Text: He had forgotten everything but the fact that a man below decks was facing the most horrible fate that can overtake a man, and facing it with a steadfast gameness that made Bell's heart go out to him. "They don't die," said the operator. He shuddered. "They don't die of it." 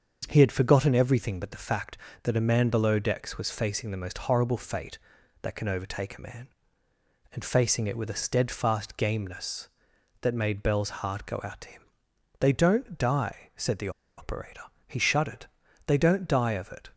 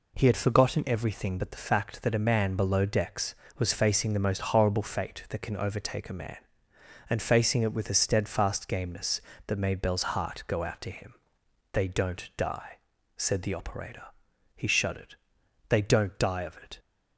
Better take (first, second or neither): second